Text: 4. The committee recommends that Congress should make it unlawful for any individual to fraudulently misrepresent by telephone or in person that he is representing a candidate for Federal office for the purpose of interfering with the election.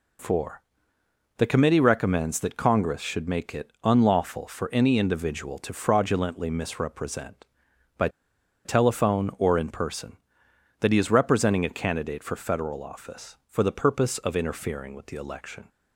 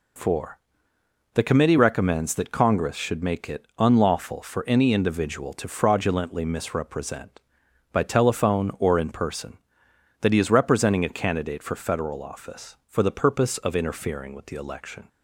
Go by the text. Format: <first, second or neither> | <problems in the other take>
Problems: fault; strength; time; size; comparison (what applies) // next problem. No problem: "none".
second | pauses between "by" and "telephone"; noticeable; at 8.0 s; 0.56 s long